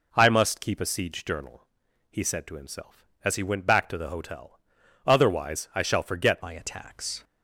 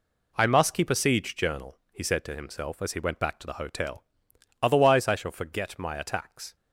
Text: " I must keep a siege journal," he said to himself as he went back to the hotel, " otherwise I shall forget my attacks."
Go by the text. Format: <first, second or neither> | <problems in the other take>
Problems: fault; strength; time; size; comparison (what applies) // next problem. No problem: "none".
second | changes voice at "my"; from 6.4 s on; 0.8 s long